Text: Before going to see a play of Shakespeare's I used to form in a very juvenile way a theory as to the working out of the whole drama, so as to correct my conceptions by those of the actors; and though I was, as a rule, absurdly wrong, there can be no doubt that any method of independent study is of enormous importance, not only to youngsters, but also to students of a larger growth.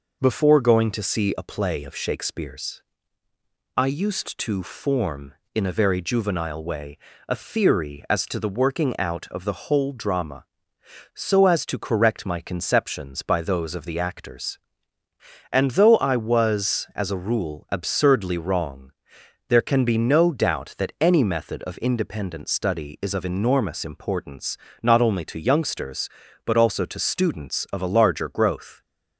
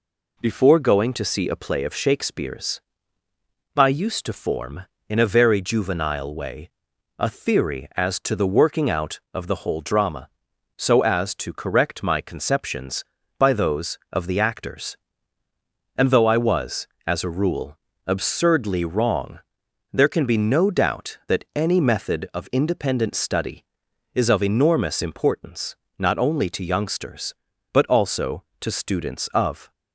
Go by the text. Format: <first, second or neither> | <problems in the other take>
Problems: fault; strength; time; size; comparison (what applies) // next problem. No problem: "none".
first | pauses between "Shakespeare's" and "I"; noticeable; at 2.7 s; 0.96 s long; noticeable in the first // pauses between "way" and "a"; noticeable; at 6.6 s; 0.48 s long; slight in the first // stops before "a larger growth"; at 29.7 s